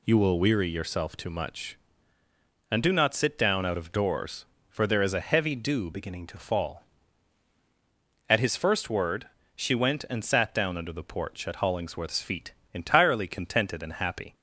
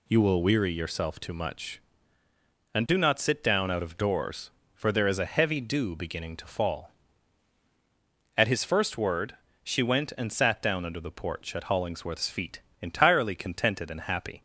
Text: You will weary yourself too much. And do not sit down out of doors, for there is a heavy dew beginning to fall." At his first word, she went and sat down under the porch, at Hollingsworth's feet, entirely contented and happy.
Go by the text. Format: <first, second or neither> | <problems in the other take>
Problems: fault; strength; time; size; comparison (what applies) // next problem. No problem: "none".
second | changes voice from "beginning" to "to"; from 5.9 to 6.3 s; 0.4 s long